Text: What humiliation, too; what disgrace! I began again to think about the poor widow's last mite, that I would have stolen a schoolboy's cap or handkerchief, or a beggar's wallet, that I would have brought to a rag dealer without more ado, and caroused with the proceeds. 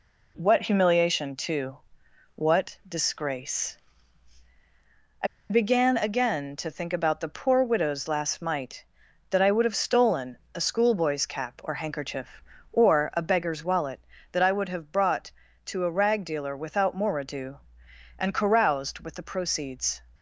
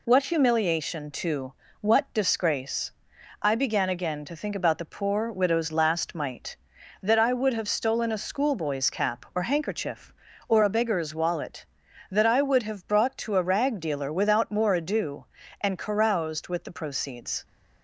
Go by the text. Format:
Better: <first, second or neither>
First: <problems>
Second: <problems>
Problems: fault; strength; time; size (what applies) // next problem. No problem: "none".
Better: second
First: pauses between "I" and "began"; slight; at 5.2 s; 0.23 s long // pauses between "stolen" and "a"; slight; at 10.3 s; 0.20 s long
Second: none